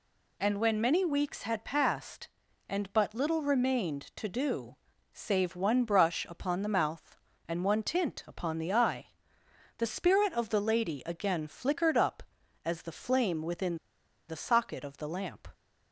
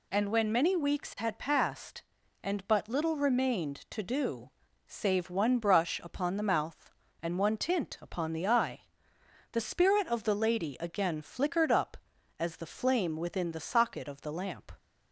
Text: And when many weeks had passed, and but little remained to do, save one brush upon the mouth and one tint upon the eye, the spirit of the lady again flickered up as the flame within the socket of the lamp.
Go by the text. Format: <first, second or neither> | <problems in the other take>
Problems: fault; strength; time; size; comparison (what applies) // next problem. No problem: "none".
second | pauses between "within" and "the"; noticeable; at 13.7 s; 0.50 s long